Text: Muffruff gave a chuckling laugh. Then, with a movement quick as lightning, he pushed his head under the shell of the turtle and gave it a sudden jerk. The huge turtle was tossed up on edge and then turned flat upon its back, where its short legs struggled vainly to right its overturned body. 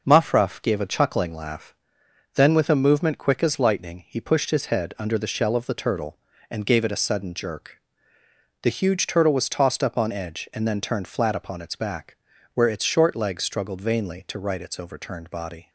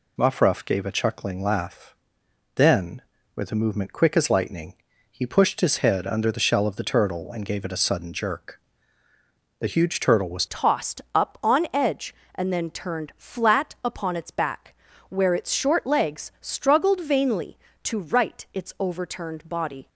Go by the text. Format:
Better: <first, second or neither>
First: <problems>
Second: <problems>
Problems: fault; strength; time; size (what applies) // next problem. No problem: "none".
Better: first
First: none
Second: changes voice at "tossed"; from 10.4 s on; 9.4 s long